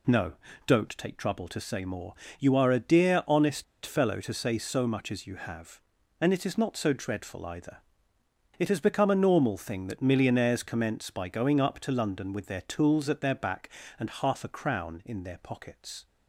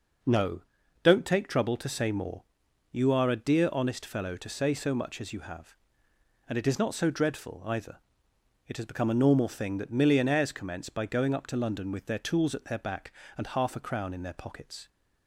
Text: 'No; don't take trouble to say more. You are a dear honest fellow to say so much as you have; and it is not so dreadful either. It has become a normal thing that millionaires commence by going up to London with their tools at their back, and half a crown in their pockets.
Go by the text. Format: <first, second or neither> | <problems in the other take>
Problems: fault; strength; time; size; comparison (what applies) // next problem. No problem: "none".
second | pauses between "honest" and "fellow"; slight; at 3.6 s; 0.21 s long